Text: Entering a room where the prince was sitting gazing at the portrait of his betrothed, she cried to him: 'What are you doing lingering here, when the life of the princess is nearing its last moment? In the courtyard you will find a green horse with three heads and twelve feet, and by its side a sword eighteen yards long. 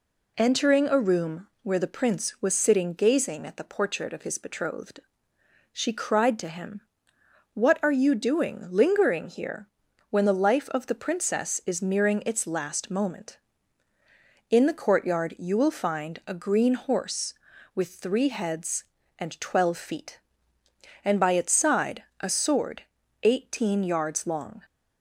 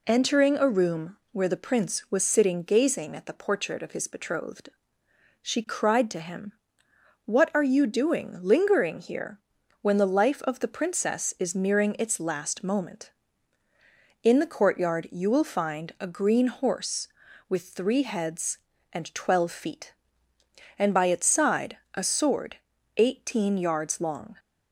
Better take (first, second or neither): neither